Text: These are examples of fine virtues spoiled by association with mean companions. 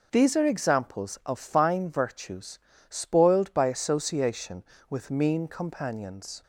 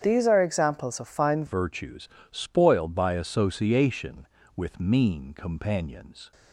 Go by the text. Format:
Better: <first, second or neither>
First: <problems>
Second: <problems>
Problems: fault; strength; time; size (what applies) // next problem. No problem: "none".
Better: first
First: pauses between "virtues" and "spoiled"; slight; at 2.5 s; 0.30 s long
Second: starts louder than the rest; strong; until 1.0 s; 8 dB // changes voice at "virtues"; from 1.4 s on; 4.9 s long // pauses between "virtues" and "spoiled"; slight; at 2.0 s; 0.24 s long